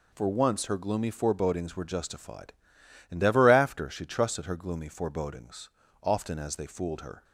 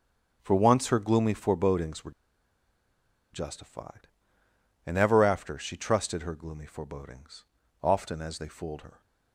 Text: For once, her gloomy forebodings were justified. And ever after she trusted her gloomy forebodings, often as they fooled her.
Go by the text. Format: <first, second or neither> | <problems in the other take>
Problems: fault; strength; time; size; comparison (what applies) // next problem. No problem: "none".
first | starts louder than the rest; strong; until 1.4 s; 7.5 dB // pauses between "were" and "justified"; at 2.1 s; 1.2 s long